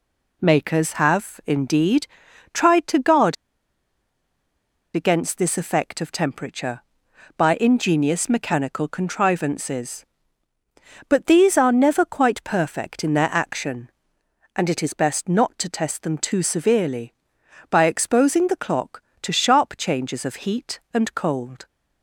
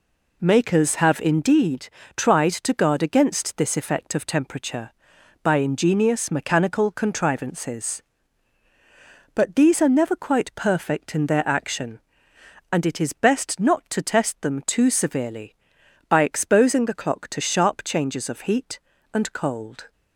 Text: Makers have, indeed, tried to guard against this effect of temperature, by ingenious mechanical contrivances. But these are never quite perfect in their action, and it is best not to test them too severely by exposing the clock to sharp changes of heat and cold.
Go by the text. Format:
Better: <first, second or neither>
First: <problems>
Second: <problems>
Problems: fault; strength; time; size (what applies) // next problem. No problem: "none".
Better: second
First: pauses between "guard" and "against"; strong; at 3.3 s; 1.6 s long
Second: none